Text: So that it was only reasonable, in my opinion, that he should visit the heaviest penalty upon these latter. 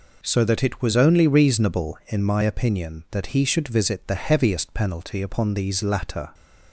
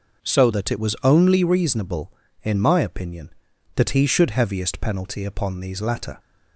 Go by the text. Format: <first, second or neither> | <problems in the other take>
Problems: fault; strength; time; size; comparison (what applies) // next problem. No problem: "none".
first | skips "visit the"; at 4.3 s